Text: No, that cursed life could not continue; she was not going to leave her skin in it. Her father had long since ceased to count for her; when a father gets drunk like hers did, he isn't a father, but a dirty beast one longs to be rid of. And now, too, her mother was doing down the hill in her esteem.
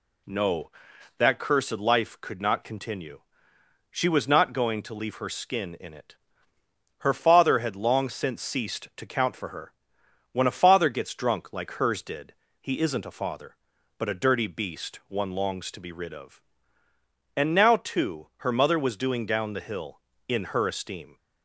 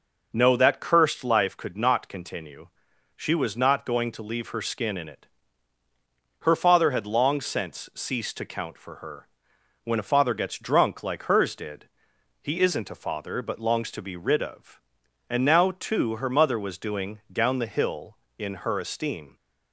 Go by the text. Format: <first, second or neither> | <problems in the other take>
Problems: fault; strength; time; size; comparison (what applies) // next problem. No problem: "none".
first | skips "a dirty beast one"; at 13.5 s